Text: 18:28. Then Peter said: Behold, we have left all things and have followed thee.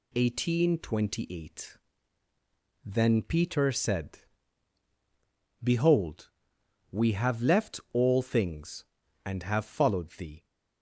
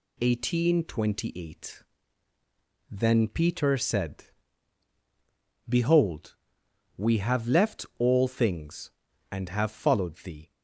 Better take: neither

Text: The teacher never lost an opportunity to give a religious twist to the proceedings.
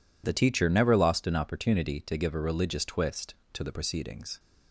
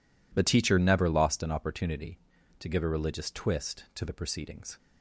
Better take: neither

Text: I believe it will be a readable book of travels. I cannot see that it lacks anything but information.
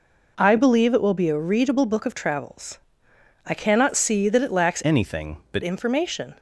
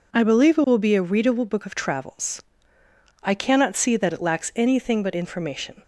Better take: second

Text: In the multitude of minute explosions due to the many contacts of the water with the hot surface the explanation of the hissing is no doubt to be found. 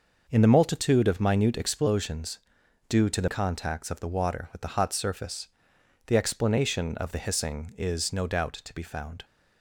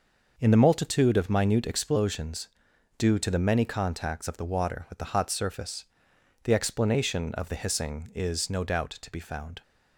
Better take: second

